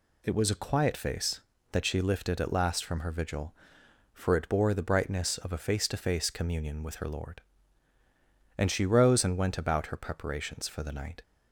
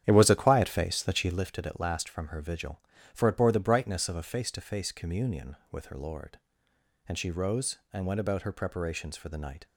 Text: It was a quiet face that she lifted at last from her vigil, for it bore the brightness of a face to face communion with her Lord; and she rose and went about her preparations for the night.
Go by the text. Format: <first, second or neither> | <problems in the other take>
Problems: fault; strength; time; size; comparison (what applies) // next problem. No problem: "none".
first | starts louder than the rest; strong; until 1.5 s; 9 dB